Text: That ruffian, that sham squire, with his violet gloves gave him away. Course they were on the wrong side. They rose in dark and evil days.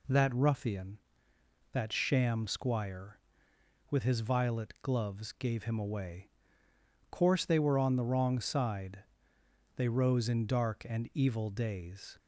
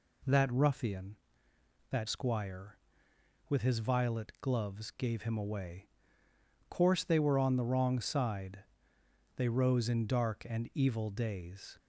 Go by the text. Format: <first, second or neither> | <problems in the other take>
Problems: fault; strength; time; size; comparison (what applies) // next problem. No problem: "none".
first | skips "sham"; at 2.0 s